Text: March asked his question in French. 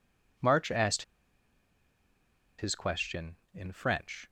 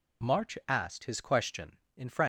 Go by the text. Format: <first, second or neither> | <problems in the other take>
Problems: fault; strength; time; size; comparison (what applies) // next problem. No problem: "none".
second | pauses between "asked" and "his"; strong; at 1.0 s; 1.5 s long